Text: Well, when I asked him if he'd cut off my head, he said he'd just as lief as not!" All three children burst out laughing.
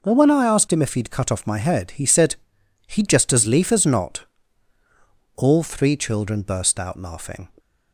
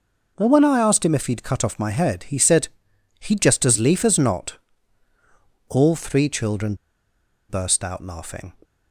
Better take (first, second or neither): first